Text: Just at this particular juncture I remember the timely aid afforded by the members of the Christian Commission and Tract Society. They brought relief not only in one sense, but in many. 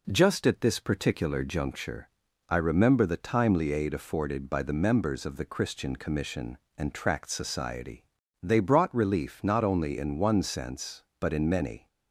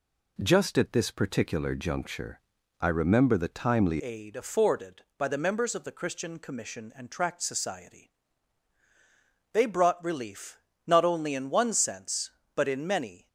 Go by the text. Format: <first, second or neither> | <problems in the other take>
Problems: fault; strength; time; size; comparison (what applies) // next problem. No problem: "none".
first | pauses between "juncture" and "I"; at 2.3 s; 0.40 s long; also in the first // changes voice at "aid"; from 3.9 s on; 9.3 s long // pauses between "relief" and "not"; slight; at 10.5 s; 0.26 s long